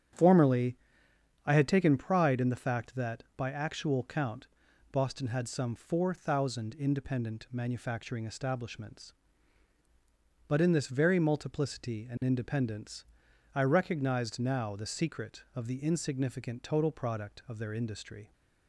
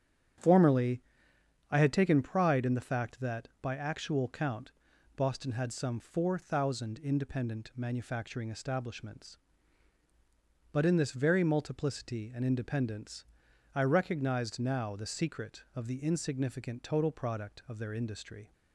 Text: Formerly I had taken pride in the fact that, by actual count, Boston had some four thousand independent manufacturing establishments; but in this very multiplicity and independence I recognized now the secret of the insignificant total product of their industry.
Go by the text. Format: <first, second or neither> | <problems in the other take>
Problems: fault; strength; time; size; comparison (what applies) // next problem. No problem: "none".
neither | starts louder than the rest; strong; the same in both // pauses between "Formerly" and "I"; noticeable; the same in both // pauses between "independence" and "I"; noticeable; the same in both